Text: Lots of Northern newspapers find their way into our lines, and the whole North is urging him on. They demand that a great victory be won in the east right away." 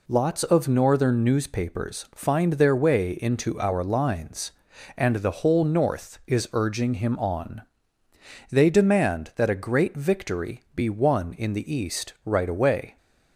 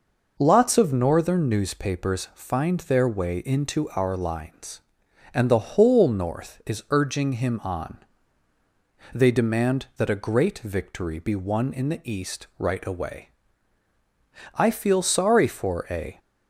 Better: first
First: none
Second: goes on to say "I feel sorry for a"; from 14.5 s on; 1.6 s long

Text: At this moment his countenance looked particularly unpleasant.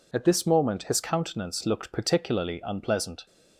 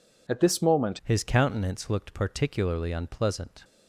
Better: first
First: none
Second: changes voice at "his"; from 1.0 s on; 2.6 s long

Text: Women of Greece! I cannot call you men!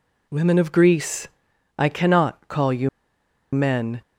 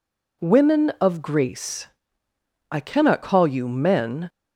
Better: second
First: pauses between "you" and "men"; noticeable; at 2.8 s; 0.64 s long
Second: none

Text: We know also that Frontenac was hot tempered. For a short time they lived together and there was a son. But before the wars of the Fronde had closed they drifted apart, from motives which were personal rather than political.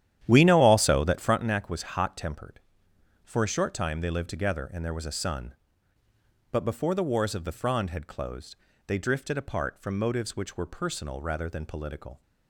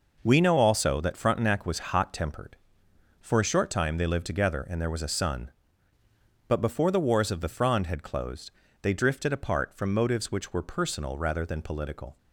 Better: second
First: starts louder than the rest; strong; until 1.4 s; 11 dB // pauses between "closed" and "they"; slight; at 8.5 s; 0.32 s long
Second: pauses between "closed" and "they"; slight; at 8.5 s; 0.32 s long

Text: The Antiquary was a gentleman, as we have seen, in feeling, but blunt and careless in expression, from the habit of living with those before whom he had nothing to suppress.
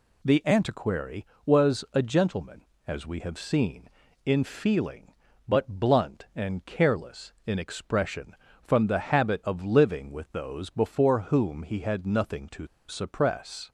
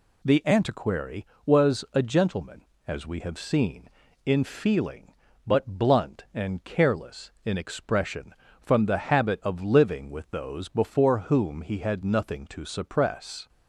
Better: second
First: pauses between "to" and "suppress"; slight; at 12.6 s; 0.22 s long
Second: none

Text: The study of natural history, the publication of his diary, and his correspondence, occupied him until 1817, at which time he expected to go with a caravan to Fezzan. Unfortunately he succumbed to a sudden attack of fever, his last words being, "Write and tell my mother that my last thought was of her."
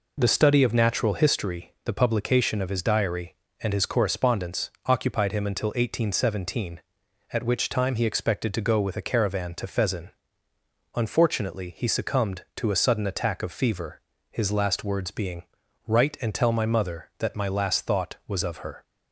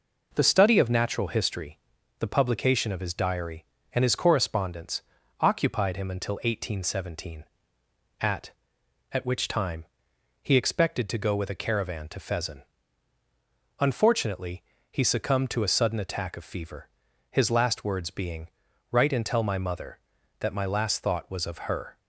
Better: first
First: none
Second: says "at" twice; at 9.1 s // pauses between "time" and "he"; noticeable; at 9.8 s; 0.58 s long // pauses between "Unfortunately" and "he"; slight; at 14.6 s; 0.28 s long

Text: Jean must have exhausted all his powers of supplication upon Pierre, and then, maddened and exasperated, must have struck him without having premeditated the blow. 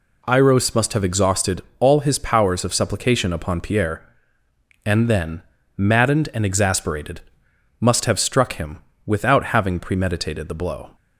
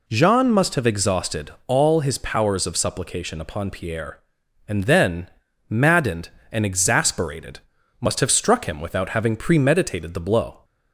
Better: second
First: says "Iros" for "Jean"; at 0.2 s // pauses between "exhausted" and "all"; slight; at 1.6 s; 0.16 s long // pauses between "him" and "without"; slight; at 8.7 s; 0.28 s long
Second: pauses between "exhausted" and "all"; slight; at 1.4 s; 0.16 s long

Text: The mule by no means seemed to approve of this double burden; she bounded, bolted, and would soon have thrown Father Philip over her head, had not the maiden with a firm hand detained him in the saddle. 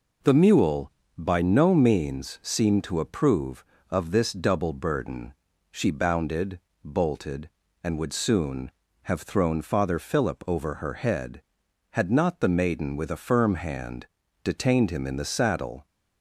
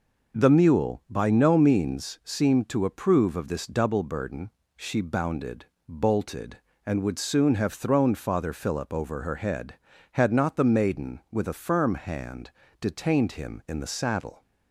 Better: neither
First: pauses between "hand" and "detained"; slight; at 14.0 s; 0.36 s long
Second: pauses between "hand" and "detained"; slight; at 12.4 s; 0.30 s long

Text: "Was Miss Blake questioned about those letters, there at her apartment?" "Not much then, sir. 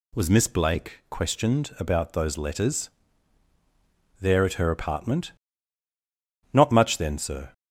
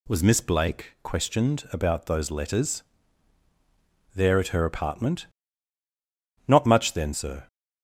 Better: neither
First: none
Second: none

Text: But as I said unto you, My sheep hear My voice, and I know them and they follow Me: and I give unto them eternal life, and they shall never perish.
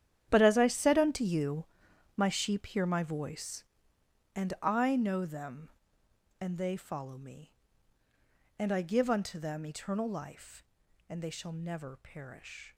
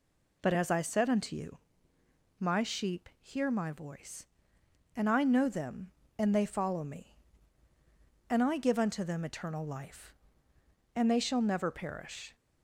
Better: second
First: gets quieter; strong; throughout; 14.5 dB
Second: none

